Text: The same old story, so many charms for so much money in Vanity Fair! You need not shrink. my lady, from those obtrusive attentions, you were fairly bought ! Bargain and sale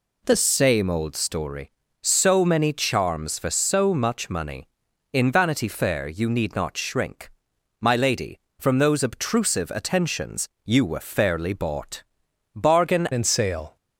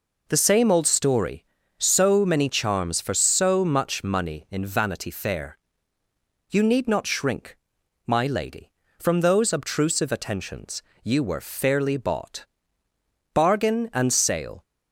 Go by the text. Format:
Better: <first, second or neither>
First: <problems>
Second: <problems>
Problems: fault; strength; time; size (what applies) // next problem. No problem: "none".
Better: second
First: changes voice at "and"; from 13.1 s on; 0.6 s long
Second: none